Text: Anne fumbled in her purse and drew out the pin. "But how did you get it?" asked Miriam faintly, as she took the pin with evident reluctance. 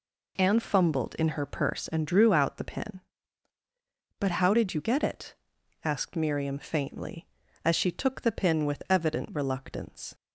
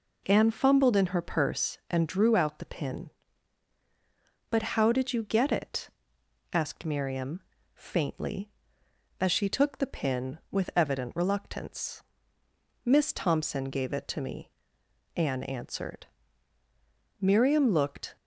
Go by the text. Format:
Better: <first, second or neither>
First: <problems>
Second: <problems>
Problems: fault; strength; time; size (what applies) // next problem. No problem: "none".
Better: first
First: none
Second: pauses between "Miriam" and "faintly"; slight; at 7.4 s; 0.32 s long // goes on to say "Miss Thompson gave it to me Anne answered Miriam looked"; strong; from 12.8 s on; 5.3 s long